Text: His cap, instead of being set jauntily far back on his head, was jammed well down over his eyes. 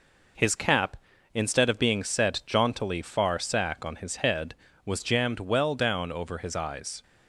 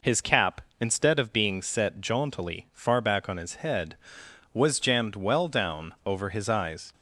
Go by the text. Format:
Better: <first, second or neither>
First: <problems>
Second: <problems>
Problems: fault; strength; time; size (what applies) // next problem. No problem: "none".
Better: second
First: says "sack" for "back"; at 3.3 s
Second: none